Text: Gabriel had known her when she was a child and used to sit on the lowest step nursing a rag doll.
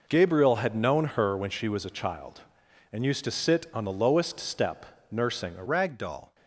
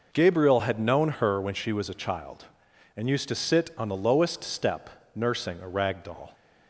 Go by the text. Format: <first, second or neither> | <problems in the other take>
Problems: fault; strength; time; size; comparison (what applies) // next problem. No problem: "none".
second | pauses between "step" and "nursing"; slight; at 4.8 s; 0.26 s long; slight in the second // changes voice at "rag"; from 5.6 s on; 0.7 s long